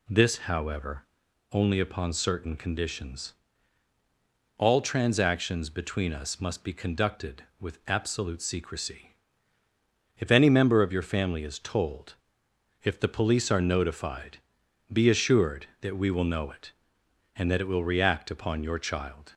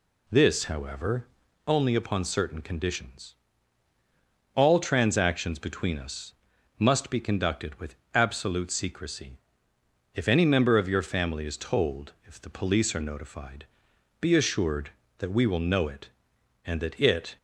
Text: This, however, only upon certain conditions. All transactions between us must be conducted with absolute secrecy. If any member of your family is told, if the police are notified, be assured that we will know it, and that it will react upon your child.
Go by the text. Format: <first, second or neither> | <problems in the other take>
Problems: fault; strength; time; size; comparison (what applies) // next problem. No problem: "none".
first | pauses between "us" and "must"; noticeable; at 6.3 s; 0.46 s long // pauses between "with" and "absolute"; slight; at 7.9 s; 0.18 s long // stops before "will react upon your child"; at 17.3 s